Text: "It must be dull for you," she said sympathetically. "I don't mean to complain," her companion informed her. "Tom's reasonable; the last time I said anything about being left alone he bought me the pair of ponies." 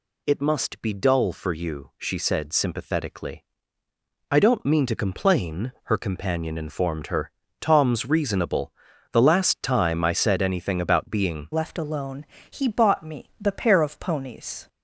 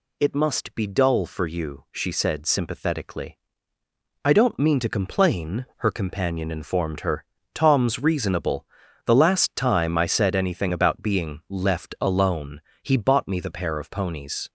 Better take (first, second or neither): second